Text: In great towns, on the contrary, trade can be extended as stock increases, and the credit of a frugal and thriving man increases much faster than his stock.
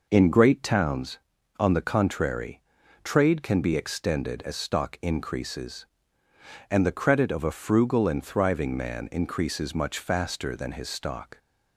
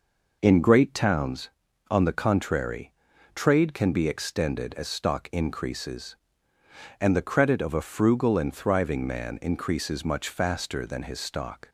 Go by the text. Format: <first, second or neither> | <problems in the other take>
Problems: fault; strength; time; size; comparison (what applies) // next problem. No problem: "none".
neither | none